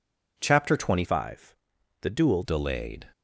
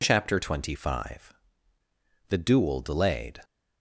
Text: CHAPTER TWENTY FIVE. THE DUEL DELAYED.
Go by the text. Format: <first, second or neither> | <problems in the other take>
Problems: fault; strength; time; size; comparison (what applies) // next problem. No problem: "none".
second | changes voice from "FIVE" to "DUEL"; from 1.0 to 2.4 s; 1.4 s long